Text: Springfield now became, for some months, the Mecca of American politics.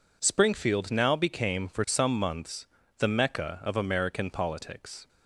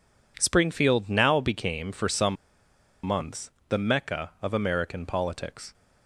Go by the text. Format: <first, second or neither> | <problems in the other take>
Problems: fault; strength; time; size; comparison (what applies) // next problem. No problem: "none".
first | pauses between "some" and "months"; noticeable; at 2.3 s; 0.68 s long